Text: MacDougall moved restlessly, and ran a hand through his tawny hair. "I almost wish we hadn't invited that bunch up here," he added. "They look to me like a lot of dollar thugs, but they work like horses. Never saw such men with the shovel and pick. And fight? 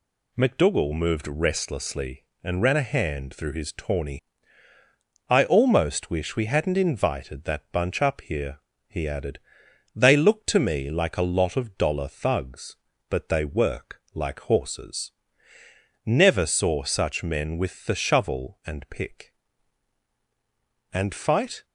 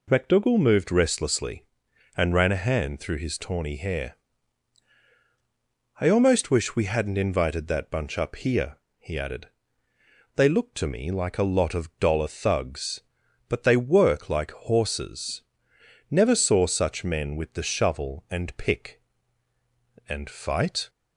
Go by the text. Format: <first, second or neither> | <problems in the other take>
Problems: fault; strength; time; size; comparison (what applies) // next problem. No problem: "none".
second | skips "hair"; at 4.7 s